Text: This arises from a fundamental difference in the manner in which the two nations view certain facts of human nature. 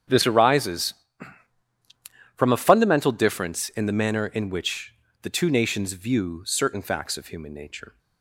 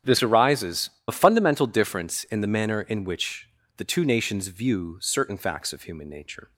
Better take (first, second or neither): first